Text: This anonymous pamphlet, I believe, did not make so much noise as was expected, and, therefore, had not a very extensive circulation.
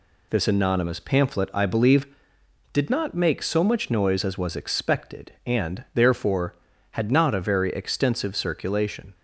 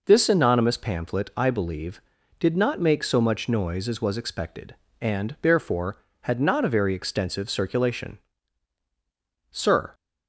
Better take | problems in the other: first | goes on to say "Sir"; slight; from 9.5 s on; 0.42 s long

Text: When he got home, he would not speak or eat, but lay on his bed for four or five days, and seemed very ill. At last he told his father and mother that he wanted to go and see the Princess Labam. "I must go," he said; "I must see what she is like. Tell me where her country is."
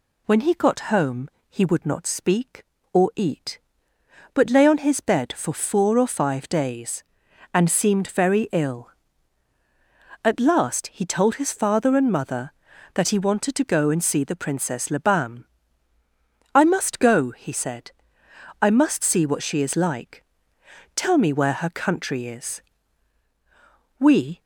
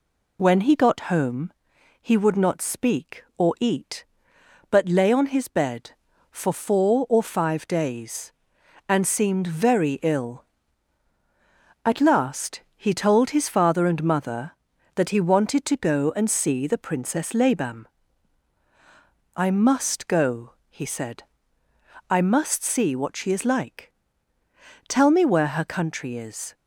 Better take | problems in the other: second | goes on to say "We"; slight; from 23.9 s on; 0.42 s long

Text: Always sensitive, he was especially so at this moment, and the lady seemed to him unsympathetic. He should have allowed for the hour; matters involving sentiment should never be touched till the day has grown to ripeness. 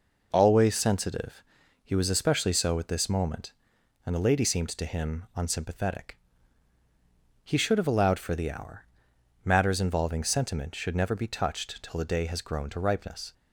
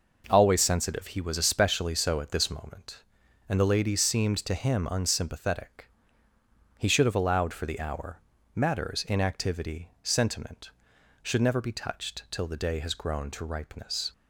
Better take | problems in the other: first | says "inactivity" for "involving"; at 9.0 s

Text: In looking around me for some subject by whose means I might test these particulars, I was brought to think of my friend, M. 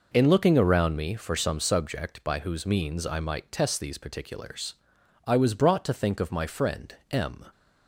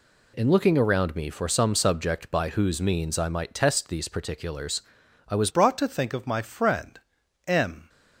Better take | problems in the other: first | changes voice at "brought"; from 5.4 s on; 2.4 s long

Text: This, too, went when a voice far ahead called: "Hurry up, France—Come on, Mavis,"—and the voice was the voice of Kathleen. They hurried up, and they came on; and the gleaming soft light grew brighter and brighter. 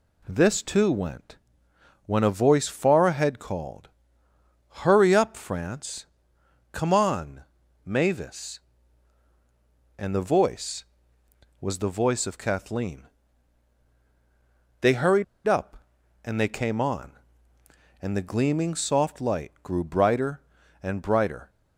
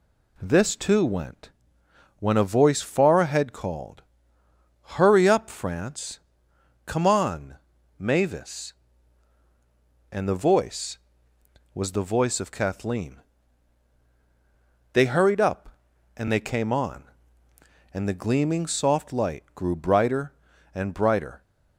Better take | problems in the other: second | pauses between "went" and "when"; noticeable; at 1.3 s; 0.70 s long; noticeable in the second // pauses between "hurried" and "up"; slight; at 15.2 s; 0.22 s long

